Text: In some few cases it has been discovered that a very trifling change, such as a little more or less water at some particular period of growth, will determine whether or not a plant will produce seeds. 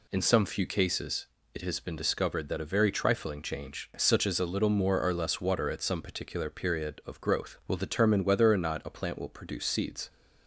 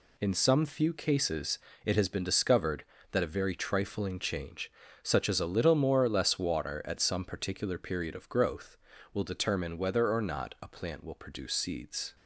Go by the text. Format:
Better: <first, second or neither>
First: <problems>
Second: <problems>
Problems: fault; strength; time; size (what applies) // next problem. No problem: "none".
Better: neither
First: pauses between "cases" and "it"; slight; at 1.2 s; 0.28 s long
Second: pauses between "cases" and "it"; slight; at 1.5 s; 0.26 s long